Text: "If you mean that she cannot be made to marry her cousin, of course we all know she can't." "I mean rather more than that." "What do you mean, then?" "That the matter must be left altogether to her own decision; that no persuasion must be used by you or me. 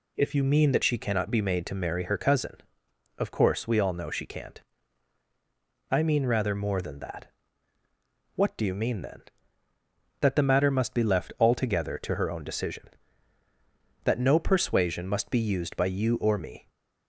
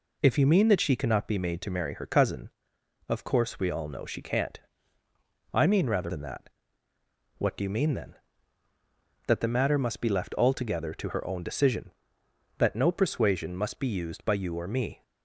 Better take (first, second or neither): first